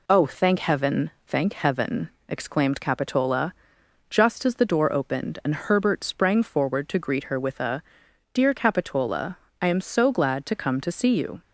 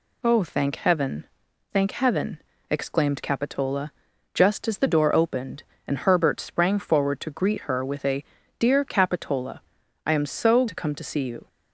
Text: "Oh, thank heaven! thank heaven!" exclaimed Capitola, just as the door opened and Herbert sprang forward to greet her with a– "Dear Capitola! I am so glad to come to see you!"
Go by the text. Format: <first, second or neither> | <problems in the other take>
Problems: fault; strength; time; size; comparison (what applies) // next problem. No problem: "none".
first | skips "glad"; at 10.6 s